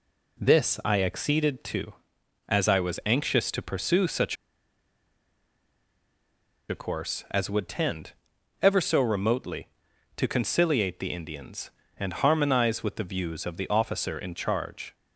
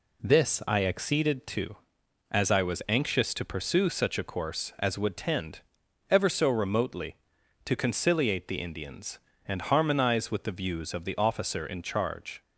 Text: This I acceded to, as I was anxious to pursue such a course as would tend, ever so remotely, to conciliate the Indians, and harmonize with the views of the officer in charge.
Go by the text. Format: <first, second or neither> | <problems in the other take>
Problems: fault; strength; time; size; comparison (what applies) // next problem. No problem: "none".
second | pauses between "such" and "a"; strong; at 4.3 s; 2.3 s long